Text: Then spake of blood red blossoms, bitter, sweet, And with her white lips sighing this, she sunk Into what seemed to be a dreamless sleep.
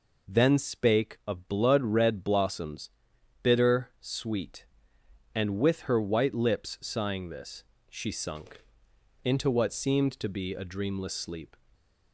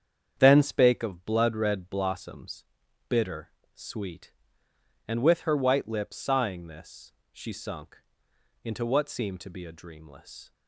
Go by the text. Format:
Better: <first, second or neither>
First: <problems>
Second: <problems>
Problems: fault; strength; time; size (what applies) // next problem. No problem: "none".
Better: first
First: pauses between "sunk" and "Into"; noticeable; at 8.6 s; 0.60 s long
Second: starts louder than the rest; strong; until 1.3 s; 8 dB // pauses between "sunk" and "Into"; noticeable; at 7.9 s; 0.66 s long // stops before "sleep"; at 10.5 s